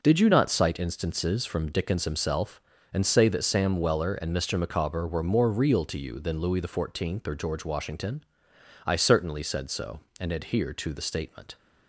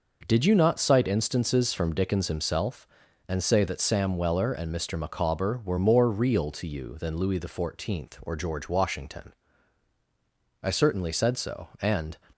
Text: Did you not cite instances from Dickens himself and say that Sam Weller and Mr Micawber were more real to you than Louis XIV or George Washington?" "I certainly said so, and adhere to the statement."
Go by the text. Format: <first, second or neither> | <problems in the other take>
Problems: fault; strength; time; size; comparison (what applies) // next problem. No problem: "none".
first | stops before "adhere to the statement"; at 12.3 s